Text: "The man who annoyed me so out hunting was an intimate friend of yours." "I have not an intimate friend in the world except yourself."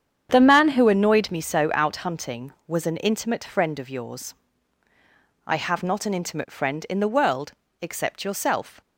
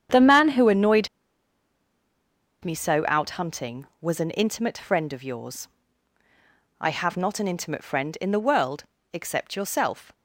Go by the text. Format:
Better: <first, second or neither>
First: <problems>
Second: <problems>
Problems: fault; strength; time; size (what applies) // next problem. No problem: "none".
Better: first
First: starts louder than the rest; strong; until 1.3 s; 8.5 dB // pauses between "world" and "except"; slight; at 7.5 s; 0.30 s long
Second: starts louder than the rest; strong; until 2.6 s; 8.5 dB // pauses between "annoyed" and "me"; strong; at 1.0 s; 1.5 s long // pauses between "world" and "except"; slight; at 8.8 s; 0.30 s long